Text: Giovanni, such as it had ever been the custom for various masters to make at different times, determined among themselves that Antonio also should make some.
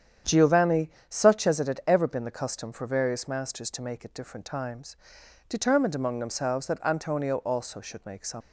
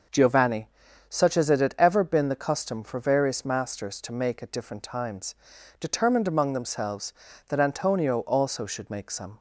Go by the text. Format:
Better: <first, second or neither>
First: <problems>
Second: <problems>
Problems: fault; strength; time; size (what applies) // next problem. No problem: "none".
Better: second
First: starts louder than the rest; strong; until 1.4 s; 9 dB // leaves "some" unfinished; at 8.4 s; 85 ms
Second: starts louder than the rest; noticeable; until 1.5 s; 6 dB